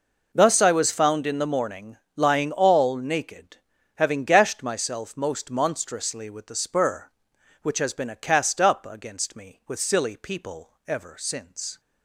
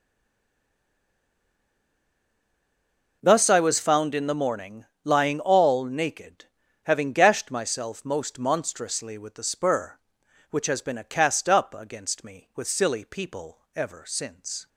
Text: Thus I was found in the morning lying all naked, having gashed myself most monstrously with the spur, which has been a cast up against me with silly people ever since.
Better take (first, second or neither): first